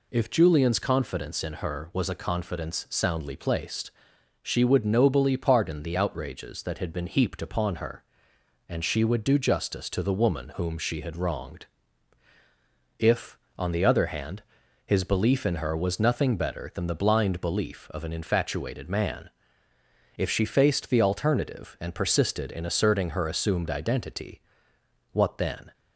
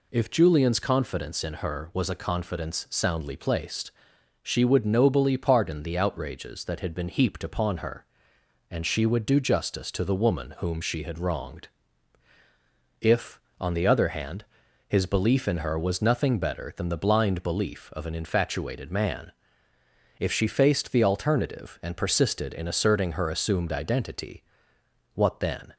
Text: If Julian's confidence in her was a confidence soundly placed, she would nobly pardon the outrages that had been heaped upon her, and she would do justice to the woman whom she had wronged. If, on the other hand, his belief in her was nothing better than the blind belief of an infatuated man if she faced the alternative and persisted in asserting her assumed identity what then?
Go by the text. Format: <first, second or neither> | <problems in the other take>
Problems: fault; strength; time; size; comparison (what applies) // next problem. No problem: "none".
neither | pauses between "man" and "if"; noticeable; the same in both // pauses between "identity" and "what"; noticeable; the same in both